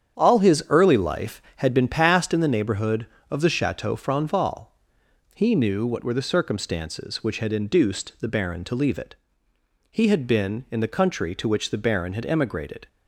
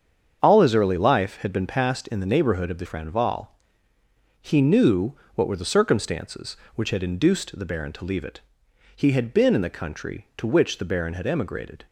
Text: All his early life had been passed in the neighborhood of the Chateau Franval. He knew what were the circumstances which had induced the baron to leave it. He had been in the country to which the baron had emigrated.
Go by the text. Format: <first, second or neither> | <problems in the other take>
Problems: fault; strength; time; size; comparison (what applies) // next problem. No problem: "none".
first | starts louder than the rest; strong; until 1.4 s; 7.5 dB; strong in the first // skips "Chateau"; at 2.8 s // pauses between "knew" and "what"; slight; at 5.1 s; 0.22 s long